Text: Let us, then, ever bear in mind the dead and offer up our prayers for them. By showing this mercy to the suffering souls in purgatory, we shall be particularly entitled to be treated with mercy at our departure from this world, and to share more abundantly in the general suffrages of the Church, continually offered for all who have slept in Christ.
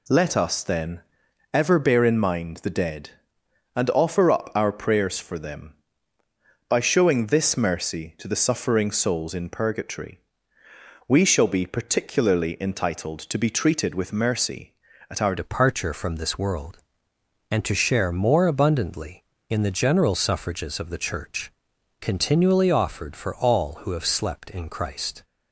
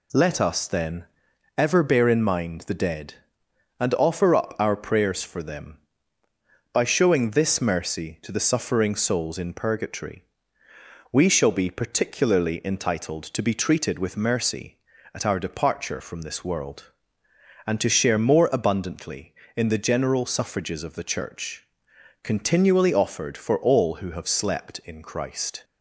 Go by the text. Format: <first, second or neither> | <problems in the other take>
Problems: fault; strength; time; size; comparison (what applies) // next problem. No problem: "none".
second | changes voice at "departure"; from 15.3 s on; 9.9 s long